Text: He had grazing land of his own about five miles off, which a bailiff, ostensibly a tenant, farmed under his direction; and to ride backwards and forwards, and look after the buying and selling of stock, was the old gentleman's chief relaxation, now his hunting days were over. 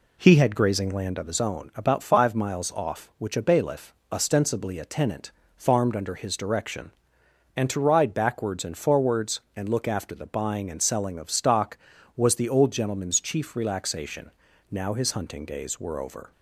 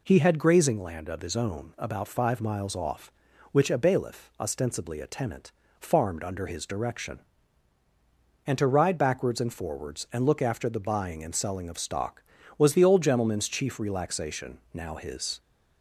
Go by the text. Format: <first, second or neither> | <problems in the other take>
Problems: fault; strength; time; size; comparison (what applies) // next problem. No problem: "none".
first | stops before "hunting days were over"; at 15.3 s